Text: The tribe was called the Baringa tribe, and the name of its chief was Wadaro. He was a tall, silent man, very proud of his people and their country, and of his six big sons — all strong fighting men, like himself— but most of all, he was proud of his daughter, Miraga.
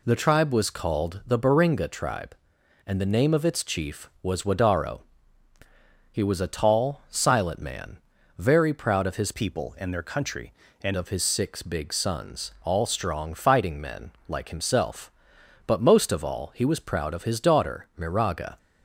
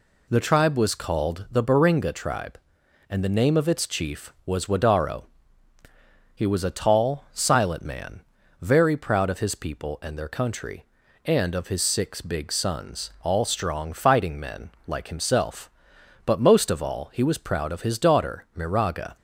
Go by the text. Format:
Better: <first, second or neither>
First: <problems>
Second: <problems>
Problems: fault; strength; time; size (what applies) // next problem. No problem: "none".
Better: second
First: changes voice from "people" to "and"; from 9.3 to 10.9 s; 1.6 s long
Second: none